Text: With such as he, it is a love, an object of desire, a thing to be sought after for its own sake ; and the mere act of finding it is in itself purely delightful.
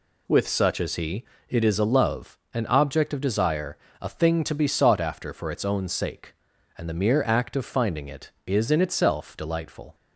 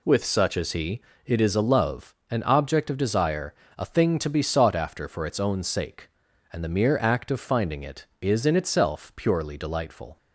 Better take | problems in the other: second | skips "purely"; at 9.3 s

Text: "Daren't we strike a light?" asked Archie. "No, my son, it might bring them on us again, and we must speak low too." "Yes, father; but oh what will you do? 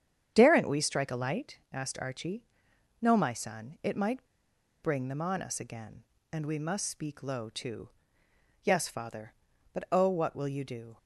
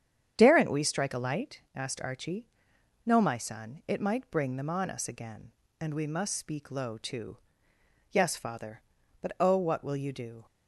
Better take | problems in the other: second | starts louder than the rest; strong; until 1.3 s; 8.5 dB; strong in the second // pauses between "might" and "bring"; noticeable; at 4.2 s; 0.57 s long

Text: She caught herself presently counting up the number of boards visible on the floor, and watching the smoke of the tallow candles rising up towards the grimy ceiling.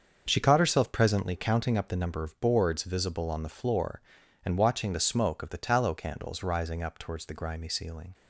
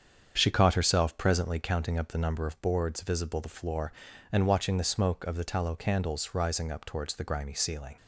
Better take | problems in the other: first | starts louder than the rest; strong; until 1.3 s; 7.5 dB; also in the first // skips "on"; at 3.4 s

